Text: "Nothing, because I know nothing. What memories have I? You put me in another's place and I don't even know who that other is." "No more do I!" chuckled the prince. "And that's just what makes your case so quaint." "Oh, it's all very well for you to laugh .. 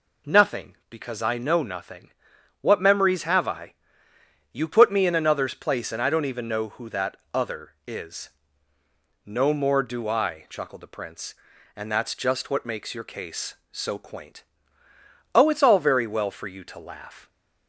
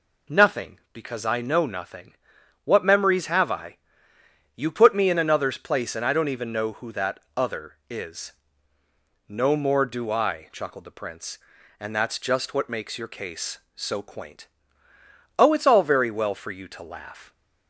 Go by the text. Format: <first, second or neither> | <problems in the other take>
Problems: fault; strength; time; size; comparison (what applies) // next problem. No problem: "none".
neither | pauses between "that" and "other"; slight; the same in both